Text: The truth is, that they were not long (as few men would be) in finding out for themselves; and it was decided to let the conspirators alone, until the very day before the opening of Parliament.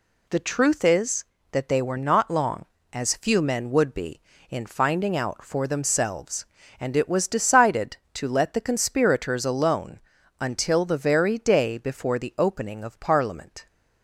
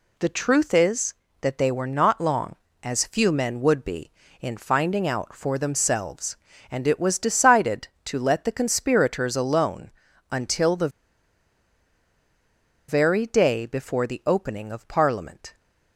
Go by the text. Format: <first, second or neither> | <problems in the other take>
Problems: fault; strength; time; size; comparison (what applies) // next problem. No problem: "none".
first | pauses between "the" and "very"; strong; at 10.8 s; 2.0 s long